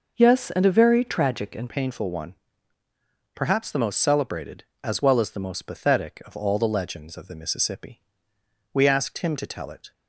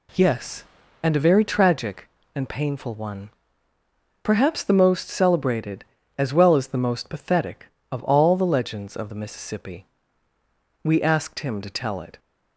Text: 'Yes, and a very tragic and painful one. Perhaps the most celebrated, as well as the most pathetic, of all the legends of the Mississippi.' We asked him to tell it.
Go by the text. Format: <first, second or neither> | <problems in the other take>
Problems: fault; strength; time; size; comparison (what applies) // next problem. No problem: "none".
second | changes voice at "painful"; from 1.6 s on; 8.3 s long